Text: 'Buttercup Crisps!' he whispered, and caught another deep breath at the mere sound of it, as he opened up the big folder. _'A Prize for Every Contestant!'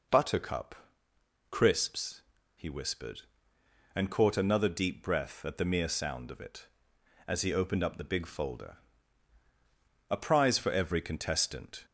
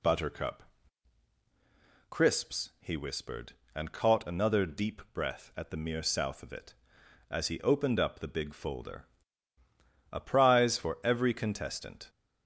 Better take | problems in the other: first | pauses between "Buttercup" and "Crisps"; strong; at 0.6 s; 1.4 s long; noticeable in the first // says "south" for "sound"; at 6.0 s

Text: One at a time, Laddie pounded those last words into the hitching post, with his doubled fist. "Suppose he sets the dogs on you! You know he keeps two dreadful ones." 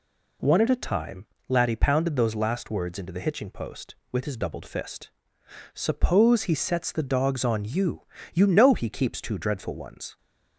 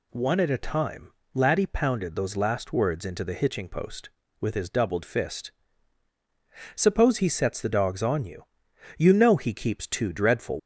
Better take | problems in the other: first | stops before "ones"; at 10.5 s

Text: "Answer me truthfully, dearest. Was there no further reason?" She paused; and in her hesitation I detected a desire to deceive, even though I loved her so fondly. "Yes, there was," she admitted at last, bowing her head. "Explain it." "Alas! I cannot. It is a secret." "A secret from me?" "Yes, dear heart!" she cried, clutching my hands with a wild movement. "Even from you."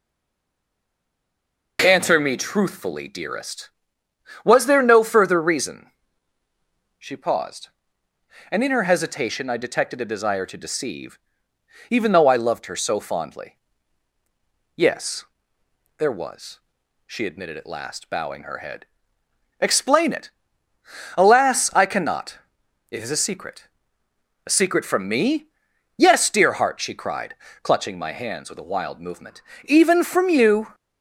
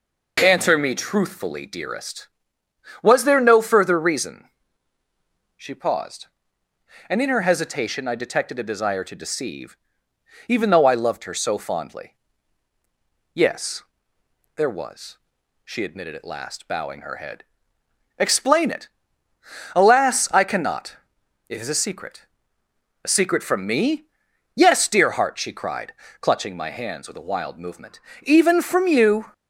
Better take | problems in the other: second | stays silent before the first word; noticeable; until 1.7 s; 1.7 s long

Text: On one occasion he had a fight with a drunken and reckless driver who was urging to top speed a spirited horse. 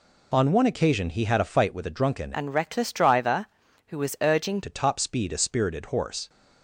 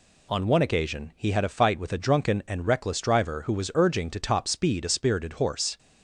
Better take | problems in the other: second | changes voice from "and" to "urging"; from 2.3 to 4.6 s; 2.3 s long

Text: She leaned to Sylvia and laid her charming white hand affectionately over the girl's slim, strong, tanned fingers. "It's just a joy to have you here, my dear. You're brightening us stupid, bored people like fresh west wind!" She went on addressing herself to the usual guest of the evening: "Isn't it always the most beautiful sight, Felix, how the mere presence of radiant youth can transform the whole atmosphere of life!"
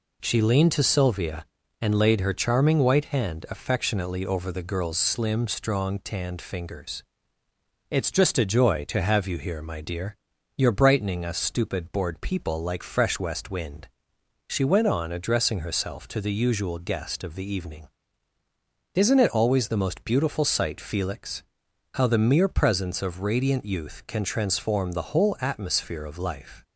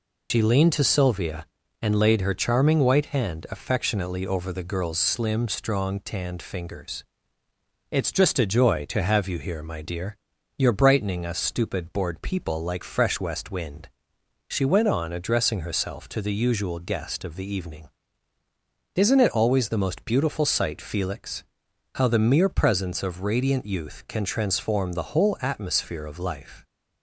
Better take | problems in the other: first | loses the start of "She"; at 0.3 s; 85 ms

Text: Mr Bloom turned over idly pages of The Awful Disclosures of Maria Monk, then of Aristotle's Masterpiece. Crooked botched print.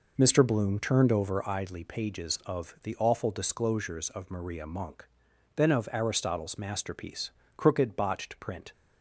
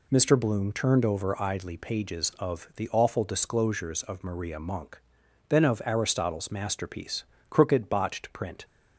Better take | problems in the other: second | starts louder than the rest; noticeable; until 1.4 s; 4.5 dB

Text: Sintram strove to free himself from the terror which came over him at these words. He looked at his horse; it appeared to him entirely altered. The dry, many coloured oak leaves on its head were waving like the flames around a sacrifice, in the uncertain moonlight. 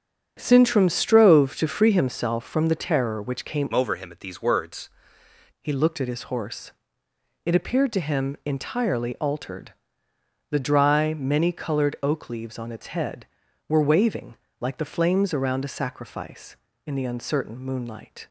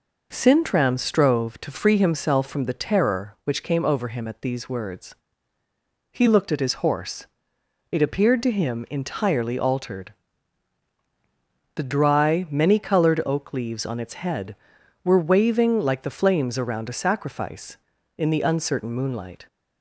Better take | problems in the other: second | starts louder than the rest; strong; until 1.3 s; 8 dB // changes voice from "over" to "words"; from 3.7 to 4.8 s; 1.1 s long // pauses between "waving" and "like"; slight; at 14.3 s; 0.24 s long

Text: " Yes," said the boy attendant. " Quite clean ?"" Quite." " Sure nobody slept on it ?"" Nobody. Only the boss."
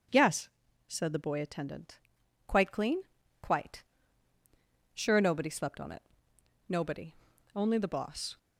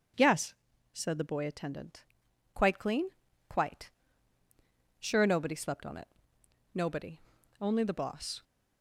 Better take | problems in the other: neither | none

